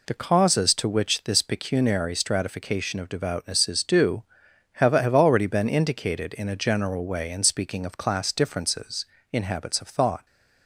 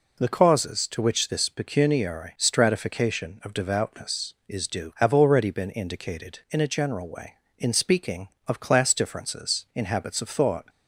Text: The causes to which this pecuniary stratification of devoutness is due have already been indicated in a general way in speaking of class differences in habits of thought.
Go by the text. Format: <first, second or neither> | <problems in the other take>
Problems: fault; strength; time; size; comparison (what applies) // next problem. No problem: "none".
second | says "have" twice; at 4.9 s